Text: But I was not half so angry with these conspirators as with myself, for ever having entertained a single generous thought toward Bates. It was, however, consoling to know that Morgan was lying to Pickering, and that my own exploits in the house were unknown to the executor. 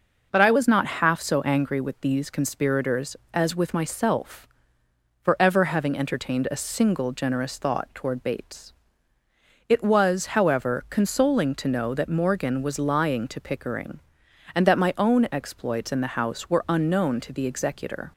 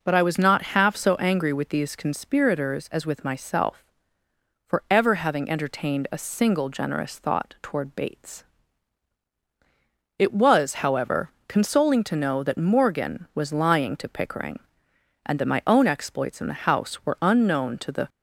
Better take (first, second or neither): first